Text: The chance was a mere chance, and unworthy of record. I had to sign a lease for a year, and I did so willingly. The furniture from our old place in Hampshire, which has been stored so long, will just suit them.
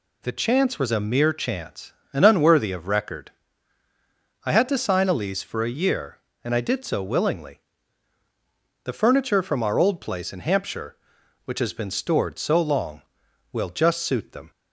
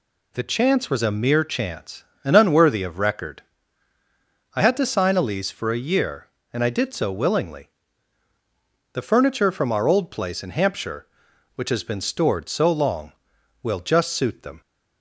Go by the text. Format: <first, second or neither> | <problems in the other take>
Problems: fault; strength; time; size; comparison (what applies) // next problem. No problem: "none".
neither | none